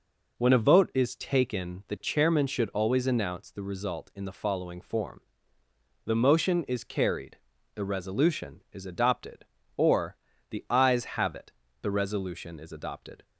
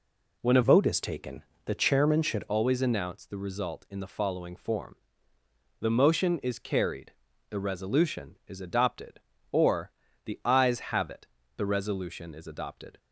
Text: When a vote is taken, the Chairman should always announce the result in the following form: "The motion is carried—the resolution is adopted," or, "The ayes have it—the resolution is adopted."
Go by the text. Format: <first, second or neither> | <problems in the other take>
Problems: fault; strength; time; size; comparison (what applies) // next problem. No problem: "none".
first | changes voice from "vote" to "should"; from 0.6 to 2.4 s; 1.8 s long